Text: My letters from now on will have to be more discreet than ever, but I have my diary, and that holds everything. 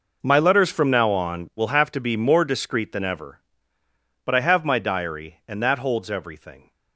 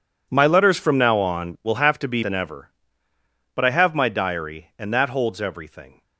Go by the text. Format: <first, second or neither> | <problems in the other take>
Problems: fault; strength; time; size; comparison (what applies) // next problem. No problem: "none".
first | skips "more discreet"; at 2.2 s